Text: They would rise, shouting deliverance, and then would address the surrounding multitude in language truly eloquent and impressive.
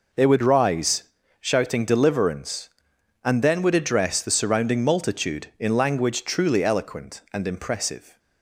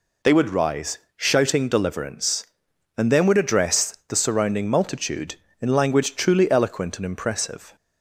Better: neither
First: none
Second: none

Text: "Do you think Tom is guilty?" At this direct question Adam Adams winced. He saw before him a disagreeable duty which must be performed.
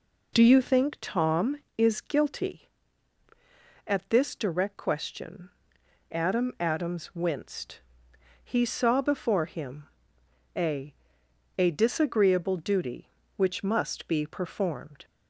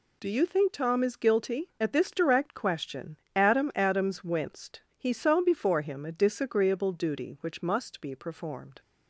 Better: second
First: pauses between "question" and "Adam"; noticeable; at 5.5 s; 0.60 s long // pauses between "him" and "a"; noticeable; at 9.8 s; 0.70 s long // says "a" twice; at 11.5 s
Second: pauses between "question" and "Adam"; slight; at 3.1 s; 0.18 s long

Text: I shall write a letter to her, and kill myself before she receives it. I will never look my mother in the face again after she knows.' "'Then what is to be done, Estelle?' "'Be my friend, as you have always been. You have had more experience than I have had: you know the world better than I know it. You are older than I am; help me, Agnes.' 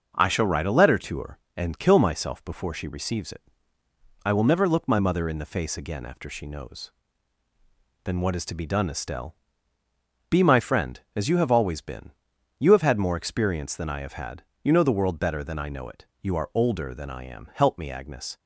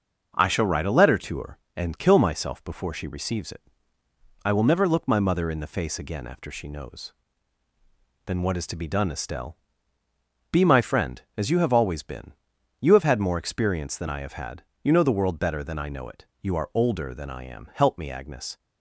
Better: neither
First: starts louder than the rest; noticeable; until 1.1 s; 6 dB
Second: starts louder than the rest; noticeable; until 1.3 s; 6 dB

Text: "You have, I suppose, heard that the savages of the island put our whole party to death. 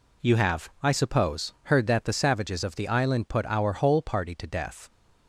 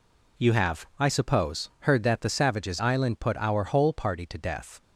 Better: first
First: none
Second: skips "of the"; at 2.7 s

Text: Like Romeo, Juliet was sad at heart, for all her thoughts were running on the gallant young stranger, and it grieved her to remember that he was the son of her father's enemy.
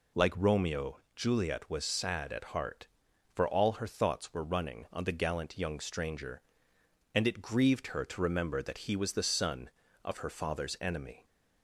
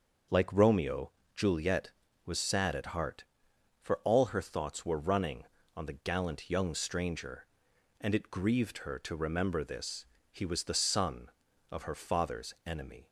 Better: first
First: none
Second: starts louder than the rest; until 1.5 s; 6.5 dB // says "this" for "that"; at 9.6 s

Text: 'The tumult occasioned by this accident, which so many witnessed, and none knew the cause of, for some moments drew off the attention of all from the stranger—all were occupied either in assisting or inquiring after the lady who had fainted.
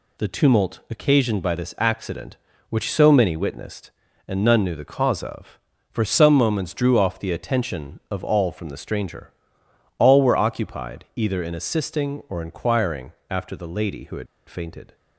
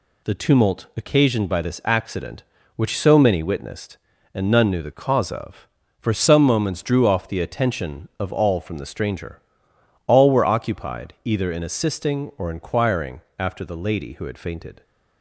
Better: second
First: pauses between "inquiring" and "after"; slight; at 13.1 s; 0.16 s long // pauses between "had" and "fainted"; slight; at 14.2 s; 0.22 s long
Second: pauses between "inquiring" and "after"; slight; at 13.2 s; 0.16 s long

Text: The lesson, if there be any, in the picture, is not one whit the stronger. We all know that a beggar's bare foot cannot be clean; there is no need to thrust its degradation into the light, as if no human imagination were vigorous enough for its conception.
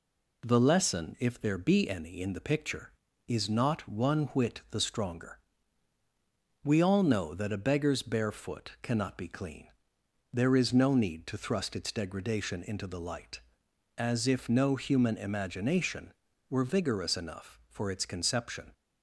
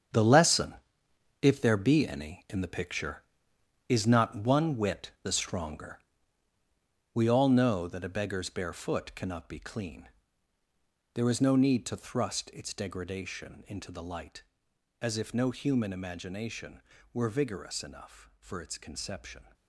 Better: first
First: none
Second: gets quieter; strong; throughout; 10 dB

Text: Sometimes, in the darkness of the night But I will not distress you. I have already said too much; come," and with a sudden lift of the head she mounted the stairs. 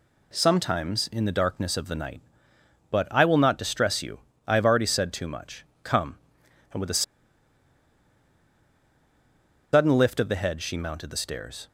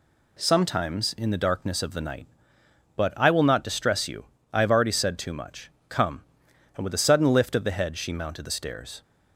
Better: second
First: pauses between "a" and "sudden"; strong; at 7.0 s; 2.7 s long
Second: none

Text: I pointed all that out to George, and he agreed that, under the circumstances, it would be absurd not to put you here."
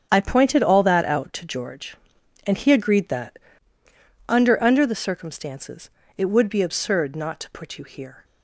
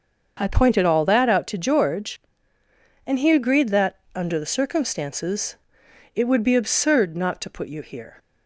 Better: second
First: starts louder than the rest; strong; until 1.1 s; 8 dB // says "under" twice; at 4.6 s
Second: starts louder than the rest; until 1.4 s; 6.5 dB

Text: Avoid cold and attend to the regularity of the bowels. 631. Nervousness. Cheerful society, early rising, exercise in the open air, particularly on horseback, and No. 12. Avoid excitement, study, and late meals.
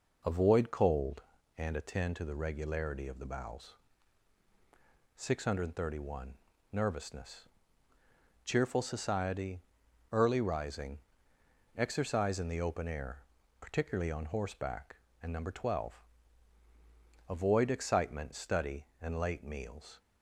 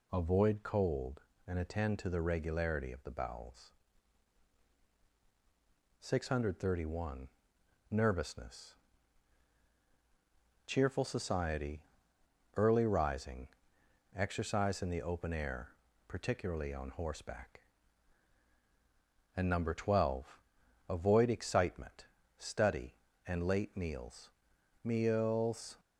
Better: first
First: none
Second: says "meals" twice; at 24.8 s

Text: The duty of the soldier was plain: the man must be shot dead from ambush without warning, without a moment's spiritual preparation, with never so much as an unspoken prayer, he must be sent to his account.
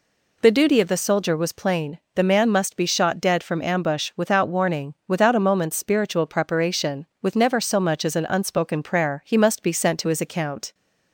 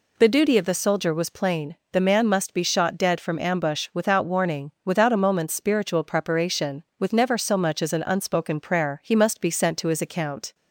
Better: neither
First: none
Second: none

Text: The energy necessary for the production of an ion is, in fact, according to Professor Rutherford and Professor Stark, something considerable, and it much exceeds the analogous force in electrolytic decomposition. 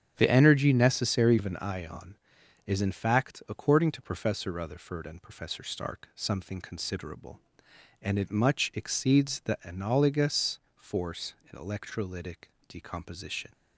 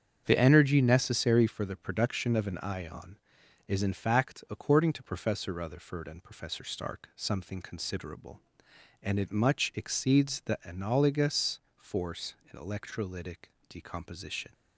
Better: second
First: starts louder than the rest; strong; until 1.1 s; 9 dB // skips "for the production"; at 1.3 s // pauses between "analogous" and "force"; slight; at 10.5 s; 0.16 s long // pauses between "electrolytic" and "decomposition"; slight; at 12.4 s; 0.20 s long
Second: starts louder than the rest; strong; until 1.2 s; 7.5 dB // pauses between "analogous" and "force"; slight; at 11.5 s; 0.16 s long // pauses between "electrolytic" and "decomposition"; slight; at 13.4 s; 0.20 s long

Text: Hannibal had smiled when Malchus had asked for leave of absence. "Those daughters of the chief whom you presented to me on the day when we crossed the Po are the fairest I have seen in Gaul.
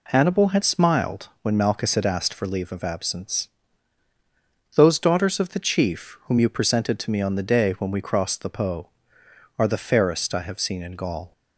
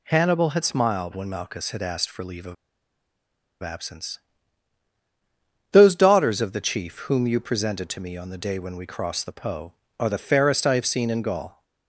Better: first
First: none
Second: pauses between "of" and "absence"; at 2.5 s; 1.0 s long

